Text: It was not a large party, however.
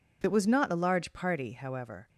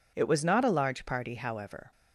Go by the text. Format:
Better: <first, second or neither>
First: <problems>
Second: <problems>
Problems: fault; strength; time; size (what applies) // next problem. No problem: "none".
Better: neither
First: none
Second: none